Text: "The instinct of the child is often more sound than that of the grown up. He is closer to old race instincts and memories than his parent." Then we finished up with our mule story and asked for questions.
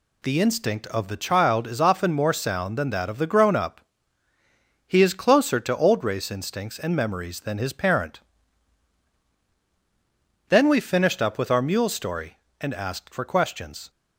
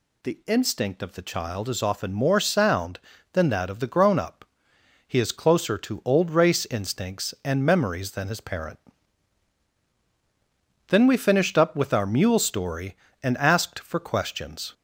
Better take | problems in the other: neither | none

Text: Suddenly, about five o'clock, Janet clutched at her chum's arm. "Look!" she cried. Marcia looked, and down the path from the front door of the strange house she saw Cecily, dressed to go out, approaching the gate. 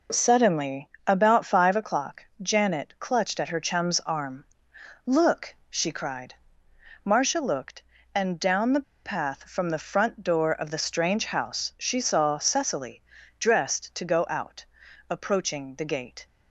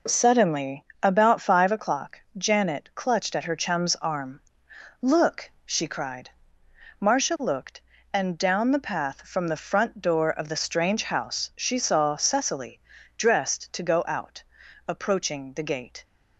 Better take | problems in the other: second | pauses between "the" and "path"; slight; at 8.8 s; 0.21 s long

